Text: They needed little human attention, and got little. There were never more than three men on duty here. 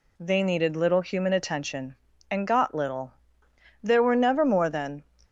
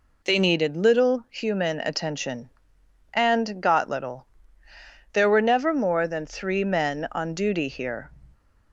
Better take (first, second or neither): second